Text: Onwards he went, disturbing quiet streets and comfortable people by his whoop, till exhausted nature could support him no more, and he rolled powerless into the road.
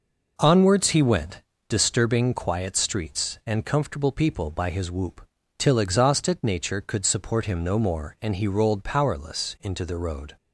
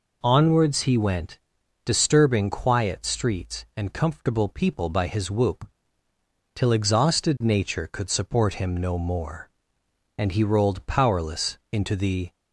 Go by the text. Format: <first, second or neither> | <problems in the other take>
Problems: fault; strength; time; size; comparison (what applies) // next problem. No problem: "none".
first | stops before "road"; at 12.3 s